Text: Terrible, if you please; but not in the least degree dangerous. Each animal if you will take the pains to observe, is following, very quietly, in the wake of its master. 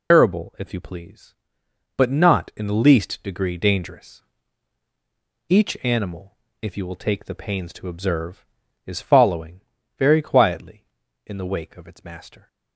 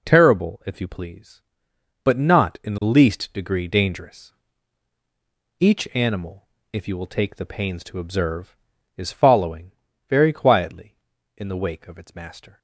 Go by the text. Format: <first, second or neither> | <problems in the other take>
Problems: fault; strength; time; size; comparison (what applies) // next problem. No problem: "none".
second | loses the start of "Terrible"; at 0.1 s; 125 ms // pauses between "animal" and "if"; slight; at 6.3 s; 0.30 s long; slight in the second